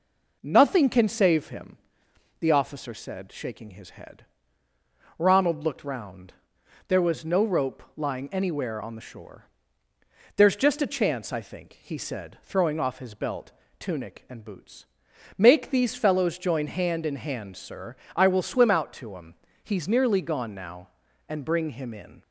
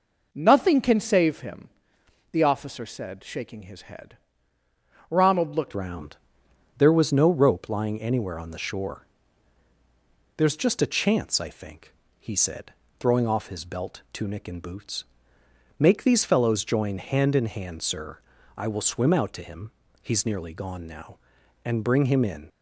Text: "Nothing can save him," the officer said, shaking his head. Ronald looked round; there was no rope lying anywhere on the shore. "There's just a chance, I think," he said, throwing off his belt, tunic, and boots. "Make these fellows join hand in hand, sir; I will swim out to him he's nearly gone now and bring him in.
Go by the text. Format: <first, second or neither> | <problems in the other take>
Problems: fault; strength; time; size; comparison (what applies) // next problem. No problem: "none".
first | changes voice at "round"; from 5.7 s on; 16.7 s long // pauses between "him" and "he's"; slight; at 19.7 s; 0.30 s long; slight in the first